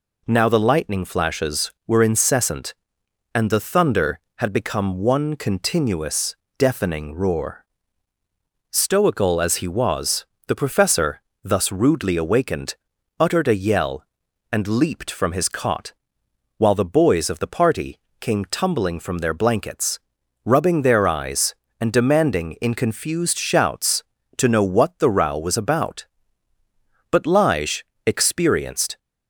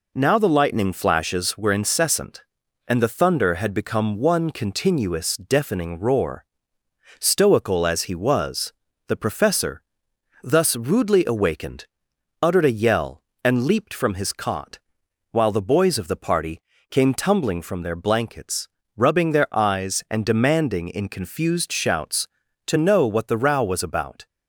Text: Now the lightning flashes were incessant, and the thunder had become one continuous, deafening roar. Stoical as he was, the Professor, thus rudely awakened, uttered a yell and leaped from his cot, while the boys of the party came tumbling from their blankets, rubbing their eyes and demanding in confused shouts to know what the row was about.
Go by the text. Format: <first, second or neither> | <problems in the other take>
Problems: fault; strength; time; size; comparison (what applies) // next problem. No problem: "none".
second | pauses between "party" and "came"; slight; at 17.9 s; 0.22 s long; slight in the second // goes on to say "But Lige experienced"; strong; from 27.0 s on; 1.8 s long